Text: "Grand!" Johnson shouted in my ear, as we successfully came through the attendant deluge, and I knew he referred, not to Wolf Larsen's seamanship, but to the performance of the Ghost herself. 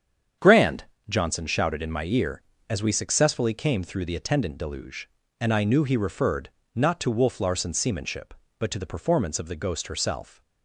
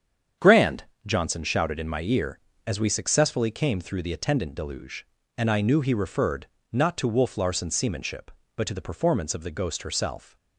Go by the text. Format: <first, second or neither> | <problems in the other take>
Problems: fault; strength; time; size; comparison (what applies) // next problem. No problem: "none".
neither | starts louder than the rest; strong; the same in both